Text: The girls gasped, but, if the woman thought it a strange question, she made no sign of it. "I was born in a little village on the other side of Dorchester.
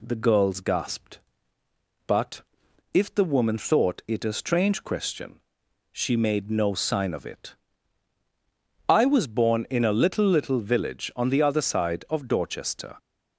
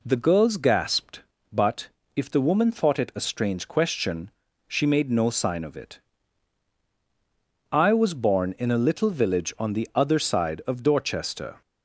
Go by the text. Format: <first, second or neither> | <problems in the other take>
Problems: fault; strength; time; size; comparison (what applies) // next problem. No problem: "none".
second | says "little" twice; at 10.2 s